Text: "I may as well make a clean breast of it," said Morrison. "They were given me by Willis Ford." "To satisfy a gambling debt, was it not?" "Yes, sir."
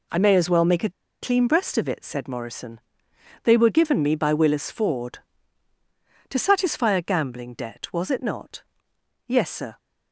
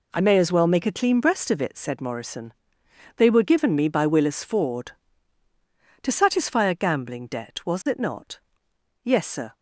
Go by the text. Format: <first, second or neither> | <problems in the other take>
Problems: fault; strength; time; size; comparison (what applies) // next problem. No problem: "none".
second | pauses between "a" and "clean"; slight; at 0.8 s; 0.31 s long